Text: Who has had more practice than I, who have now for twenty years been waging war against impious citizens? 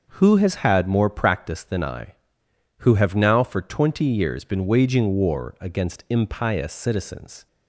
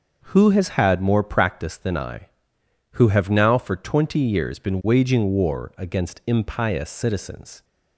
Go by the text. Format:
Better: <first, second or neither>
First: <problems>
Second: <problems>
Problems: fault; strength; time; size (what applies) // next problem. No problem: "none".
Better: neither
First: starts louder than the rest; noticeable; until 1.1 s; 6 dB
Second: starts louder than the rest; noticeable; until 1.2 s; 6 dB